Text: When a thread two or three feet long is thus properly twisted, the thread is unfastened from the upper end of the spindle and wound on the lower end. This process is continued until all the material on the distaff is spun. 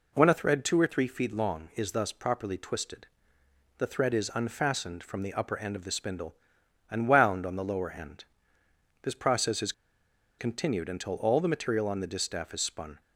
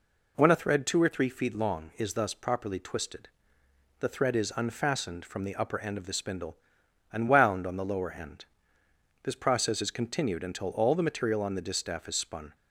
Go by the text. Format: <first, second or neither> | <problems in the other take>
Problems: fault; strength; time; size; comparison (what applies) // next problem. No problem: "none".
second | pauses between "is" and "continued"; noticeable; at 9.7 s; 0.66 s long